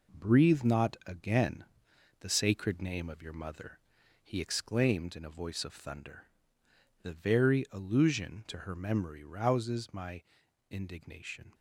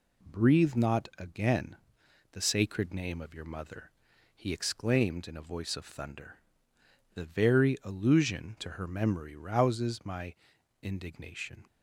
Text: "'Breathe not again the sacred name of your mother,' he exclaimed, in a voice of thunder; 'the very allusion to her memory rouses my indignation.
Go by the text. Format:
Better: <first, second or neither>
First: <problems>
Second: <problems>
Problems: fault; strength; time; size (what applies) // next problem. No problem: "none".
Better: second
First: gets quieter; noticeable; throughout; 6 dB // pauses between "again" and "the"; noticeable; at 1.6 s; 0.56 s long // pauses between "my" and "indignation"; at 10.2 s; 0.44 s long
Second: pauses between "again" and "the"; noticeable; at 1.7 s; 0.56 s long // pauses between "my" and "indignation"; at 10.3 s; 0.44 s long